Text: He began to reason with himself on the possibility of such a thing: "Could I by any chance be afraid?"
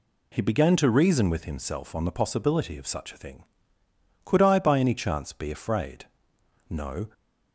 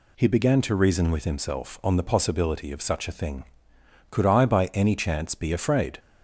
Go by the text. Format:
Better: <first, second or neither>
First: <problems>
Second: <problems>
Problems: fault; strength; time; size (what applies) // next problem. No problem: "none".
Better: second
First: goes on to say "No"; slight; from 6.7 s on; 0.42 s long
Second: none